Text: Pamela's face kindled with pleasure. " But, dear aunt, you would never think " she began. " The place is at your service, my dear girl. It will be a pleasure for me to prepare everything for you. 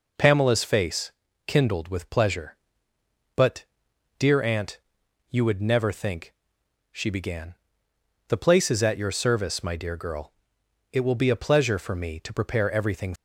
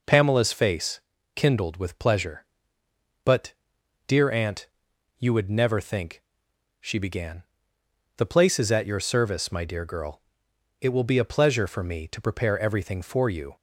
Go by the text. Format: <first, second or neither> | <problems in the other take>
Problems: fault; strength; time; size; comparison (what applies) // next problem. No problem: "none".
second | pauses between "face" and "kindled"; slight; at 1.1 s; 0.34 s long; slight in the second // stops before "for you"; at 13.1 s